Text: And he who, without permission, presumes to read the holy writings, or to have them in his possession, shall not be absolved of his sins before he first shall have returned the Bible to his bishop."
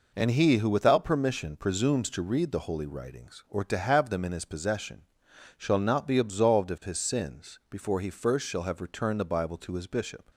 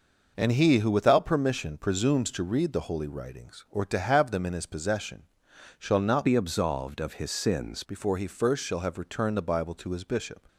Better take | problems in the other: first | changes voice from "be" to "sins"; from 6.2 to 7.8 s; 1.6 s long

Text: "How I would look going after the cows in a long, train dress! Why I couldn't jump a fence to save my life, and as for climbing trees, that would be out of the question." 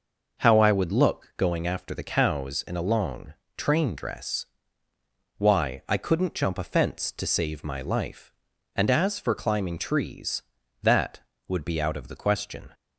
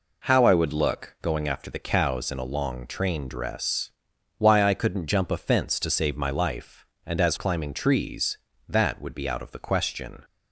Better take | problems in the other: first | skips "for"; at 7.3 s

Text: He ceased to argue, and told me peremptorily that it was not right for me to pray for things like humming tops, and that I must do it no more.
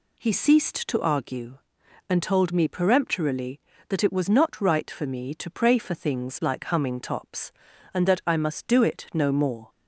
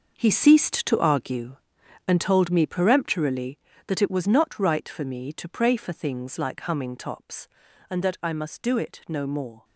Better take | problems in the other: first | gets quieter; strong; throughout; 11 dB

